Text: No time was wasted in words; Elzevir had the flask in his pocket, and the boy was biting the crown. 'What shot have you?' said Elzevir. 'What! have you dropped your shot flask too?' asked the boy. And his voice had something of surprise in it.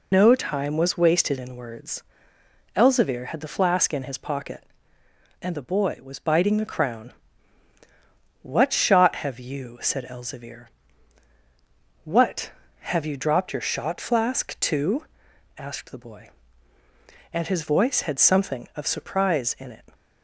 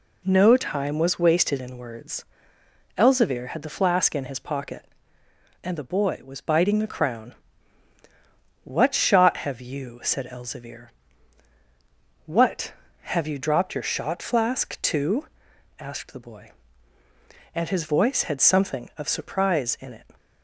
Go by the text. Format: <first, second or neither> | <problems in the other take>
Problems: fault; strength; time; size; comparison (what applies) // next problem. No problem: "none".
second | loses the start of "No"; at 0.1 s; 90 ms